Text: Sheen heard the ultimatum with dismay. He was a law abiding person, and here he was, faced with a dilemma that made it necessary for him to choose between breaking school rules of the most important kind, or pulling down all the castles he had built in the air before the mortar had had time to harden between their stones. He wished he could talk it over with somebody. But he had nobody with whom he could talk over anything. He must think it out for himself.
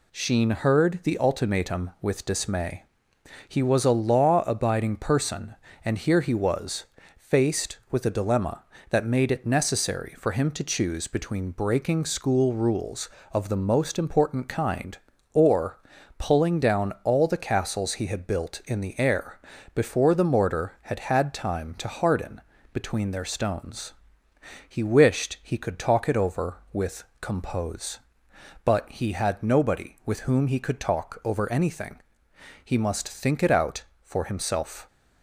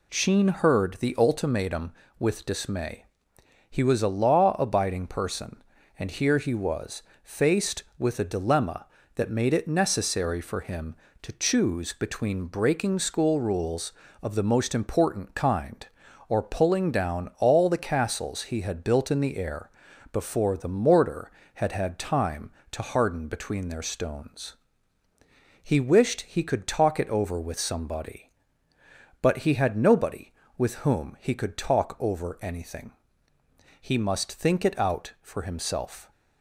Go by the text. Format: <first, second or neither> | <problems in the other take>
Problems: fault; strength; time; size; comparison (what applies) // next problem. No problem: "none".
second | pauses between "or" and "pulling"; at 15.7 s; 0.40 s long // pauses between "air" and "before"; slight; at 19.3 s; 0.36 s long; also in the second // pauses between "harden" and "between"; slight; at 22.4 s; 0.32 s long // says "compose" for "somebody"; at 27.2 s